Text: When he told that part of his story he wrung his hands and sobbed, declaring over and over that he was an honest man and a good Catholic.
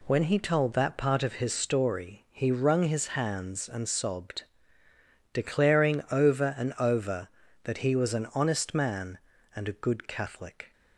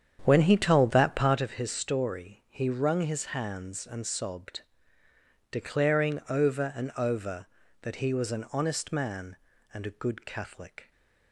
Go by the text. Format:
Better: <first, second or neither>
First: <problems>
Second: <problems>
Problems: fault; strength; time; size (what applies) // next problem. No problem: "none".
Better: first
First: none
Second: starts louder than the rest; strong; until 1.5 s; 8.5 dB